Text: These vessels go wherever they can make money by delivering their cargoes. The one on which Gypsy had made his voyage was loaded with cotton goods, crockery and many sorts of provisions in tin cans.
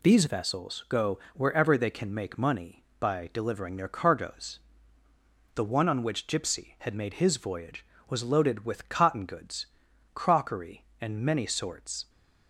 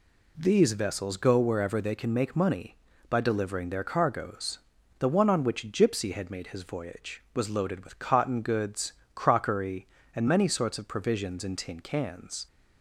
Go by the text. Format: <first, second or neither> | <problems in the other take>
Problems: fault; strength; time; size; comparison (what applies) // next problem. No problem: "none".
second | stops before "of provisions in tin cans"; at 12.0 s